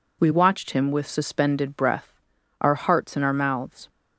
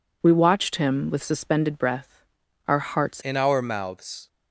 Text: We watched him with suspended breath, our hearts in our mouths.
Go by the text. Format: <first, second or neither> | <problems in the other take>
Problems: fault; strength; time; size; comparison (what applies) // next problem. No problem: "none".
first | changes voice at "in"; from 3.2 s on; 1.0 s long